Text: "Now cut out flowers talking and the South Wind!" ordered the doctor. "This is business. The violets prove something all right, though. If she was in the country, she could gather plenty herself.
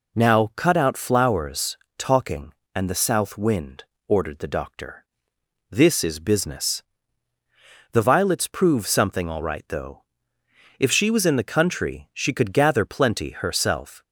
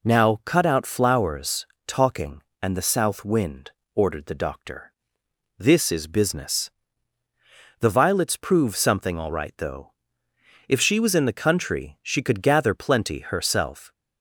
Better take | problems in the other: neither | pauses between "flowers" and "talking"; slight; the same in both

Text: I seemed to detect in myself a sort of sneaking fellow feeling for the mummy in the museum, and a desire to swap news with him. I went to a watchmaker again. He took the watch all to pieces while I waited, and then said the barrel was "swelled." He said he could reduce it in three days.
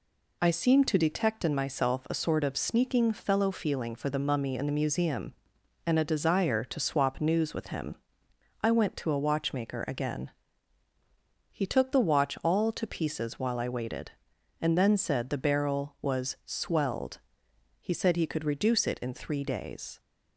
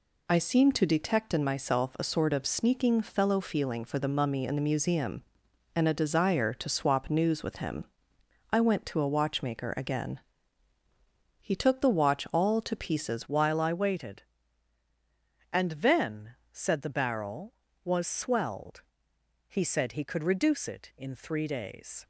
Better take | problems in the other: first | changes voice at "while"; from 13.2 s on; 8.8 s long // pauses between "then" and "said"; slight; at 16.3 s; 0.18 s long

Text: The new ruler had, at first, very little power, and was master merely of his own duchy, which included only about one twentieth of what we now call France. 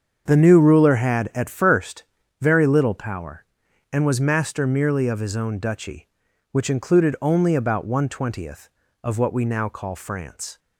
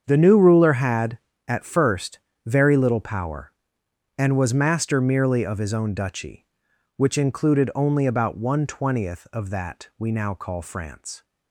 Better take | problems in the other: first | starts louder than the rest; strong; until 1.0 s; 7.5 dB; strong in the first // says "that" for "what"; at 9.4 s

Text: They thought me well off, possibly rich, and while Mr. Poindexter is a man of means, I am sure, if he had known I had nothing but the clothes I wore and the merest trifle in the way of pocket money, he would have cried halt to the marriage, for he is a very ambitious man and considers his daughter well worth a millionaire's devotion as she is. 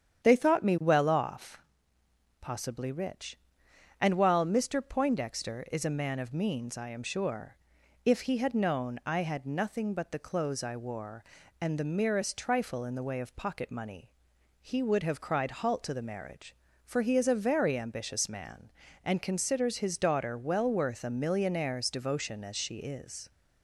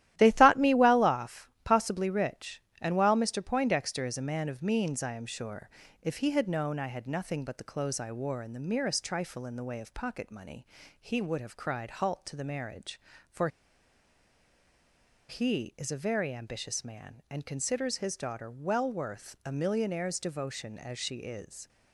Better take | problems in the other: first | starts louder than the rest; strong; until 1.1 s; 13.5 dB; strong in the first // pauses between "for" and "he"; strong; at 13.4 s; 1.8 s long

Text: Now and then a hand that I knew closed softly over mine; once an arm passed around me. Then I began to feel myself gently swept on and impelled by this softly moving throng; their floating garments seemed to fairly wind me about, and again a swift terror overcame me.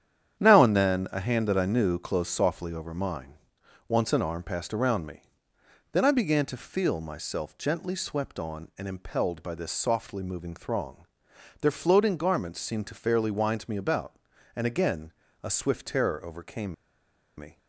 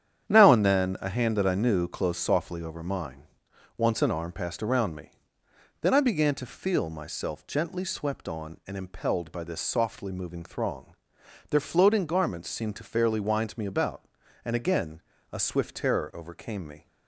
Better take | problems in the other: second | starts louder than the rest; strong; until 1.4 s; 9.5 dB; strong in the second // pauses between "again" and "a"; slight; at 15.1 s; 0.28 s long; slight in the second // pauses between "overcame" and "me"; noticeable; at 16.7 s; 0.63 s long

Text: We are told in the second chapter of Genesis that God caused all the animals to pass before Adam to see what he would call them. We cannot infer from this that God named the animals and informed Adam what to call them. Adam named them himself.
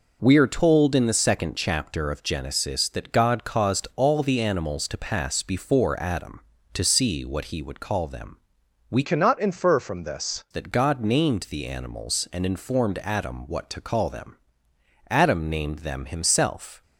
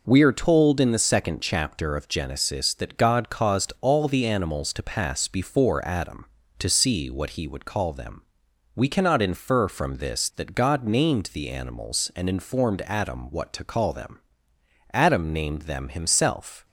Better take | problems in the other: second | changes voice from "cannot" to "this"; from 9.0 to 10.4 s; 1.4 s long

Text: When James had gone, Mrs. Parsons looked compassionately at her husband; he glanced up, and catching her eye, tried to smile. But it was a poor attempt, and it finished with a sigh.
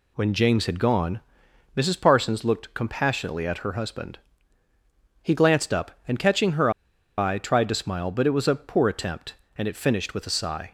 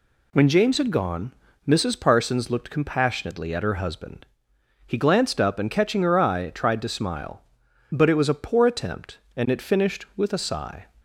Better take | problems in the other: second | pauses between "her" and "eye"; noticeable; at 6.6 s; 0.47 s long

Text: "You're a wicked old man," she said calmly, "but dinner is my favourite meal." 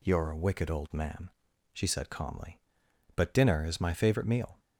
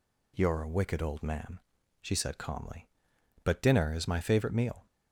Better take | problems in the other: neither | none

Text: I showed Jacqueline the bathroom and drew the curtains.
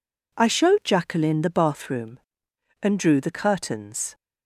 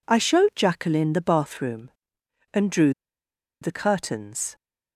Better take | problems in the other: first | pauses between "drew" and "the"; noticeable; at 2.9 s; 0.70 s long

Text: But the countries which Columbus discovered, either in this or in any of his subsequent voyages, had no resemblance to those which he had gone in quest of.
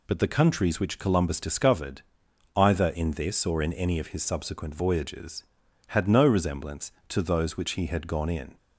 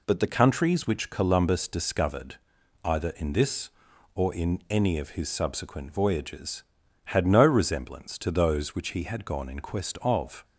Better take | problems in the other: second | stops before "quest of"; at 8.5 s

